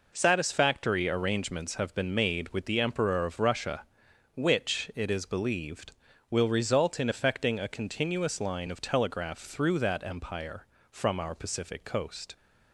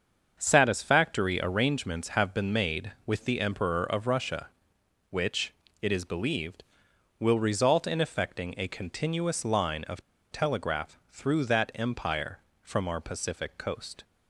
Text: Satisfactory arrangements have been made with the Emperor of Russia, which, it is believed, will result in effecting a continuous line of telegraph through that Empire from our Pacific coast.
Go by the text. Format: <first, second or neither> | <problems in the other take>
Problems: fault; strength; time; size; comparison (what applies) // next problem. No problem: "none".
first | starts louder than the rest; until 1.4 s; 7 dB // pauses between "of" and "telegraph"; slight; at 9.9 s; 0.32 s long